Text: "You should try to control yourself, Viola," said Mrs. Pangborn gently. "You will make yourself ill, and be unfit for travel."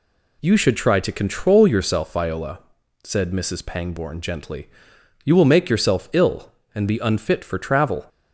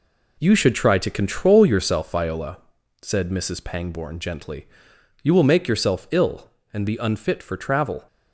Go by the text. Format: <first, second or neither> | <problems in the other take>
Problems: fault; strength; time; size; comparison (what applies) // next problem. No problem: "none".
first | gets quieter; strong; throughout; 8 dB